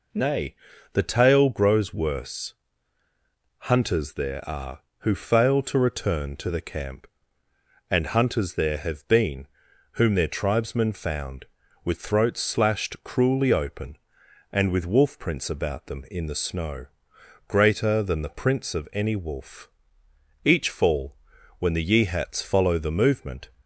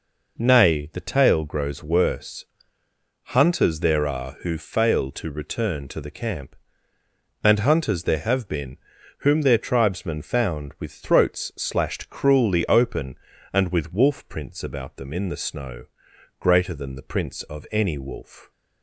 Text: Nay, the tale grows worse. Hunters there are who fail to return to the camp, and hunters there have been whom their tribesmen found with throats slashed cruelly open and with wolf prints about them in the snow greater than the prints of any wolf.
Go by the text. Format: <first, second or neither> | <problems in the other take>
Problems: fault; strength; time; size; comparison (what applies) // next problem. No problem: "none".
second | pauses between "been" and "whom"; noticeable; at 9.4 s; 0.46 s long; also in the second // pauses between "snow" and "greater"; noticeable; at 16.8 s; 0.62 s long; noticeable in the second // goes on to say "Each fall when the Yeehats follow the movement"; strong; from 20.4 s on; 3.0 s long